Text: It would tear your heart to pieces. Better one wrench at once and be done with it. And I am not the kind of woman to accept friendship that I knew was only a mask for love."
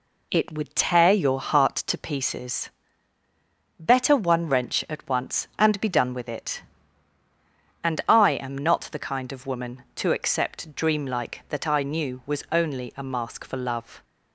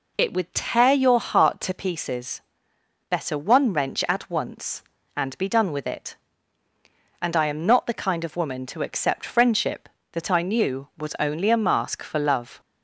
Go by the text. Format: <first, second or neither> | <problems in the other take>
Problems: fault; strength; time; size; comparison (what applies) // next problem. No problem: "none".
second | says "dreamlike" for "friendship"; at 10.7 s